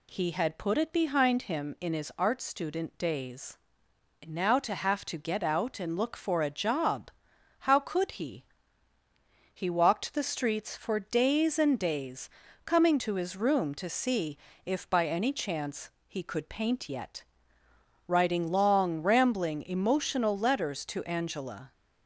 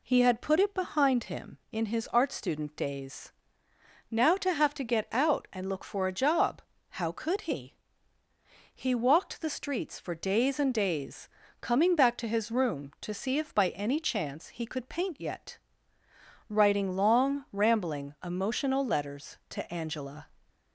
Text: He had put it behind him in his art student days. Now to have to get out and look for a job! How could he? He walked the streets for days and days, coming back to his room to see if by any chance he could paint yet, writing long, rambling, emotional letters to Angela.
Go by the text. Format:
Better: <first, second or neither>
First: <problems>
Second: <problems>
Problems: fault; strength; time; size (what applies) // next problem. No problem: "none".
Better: second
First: skips "back"; at 12.9 s // pauses between "see" and "if"; slight; at 14.3 s; 0.28 s long // pauses between "chance" and "he"; slight; at 15.8 s; 0.18 s long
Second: none